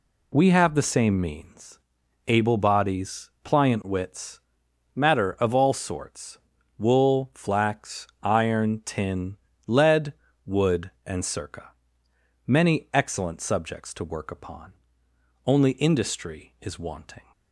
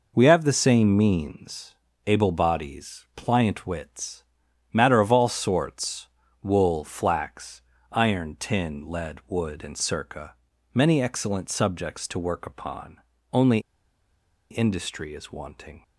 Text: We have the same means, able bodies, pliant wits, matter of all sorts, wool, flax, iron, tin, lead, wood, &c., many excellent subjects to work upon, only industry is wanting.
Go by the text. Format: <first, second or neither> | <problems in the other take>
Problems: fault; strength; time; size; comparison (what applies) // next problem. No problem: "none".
first | pauses between "only" and "industry"; noticeable; at 13.5 s; 0.91 s long